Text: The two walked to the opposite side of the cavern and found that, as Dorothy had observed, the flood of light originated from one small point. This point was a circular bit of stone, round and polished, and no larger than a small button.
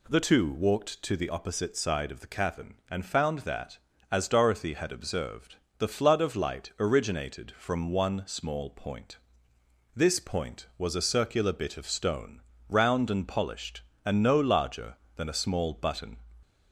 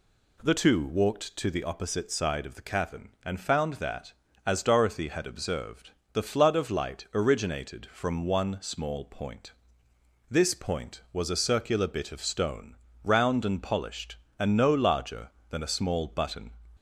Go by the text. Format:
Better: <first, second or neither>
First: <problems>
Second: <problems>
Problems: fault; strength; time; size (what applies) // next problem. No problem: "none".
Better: neither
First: none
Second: none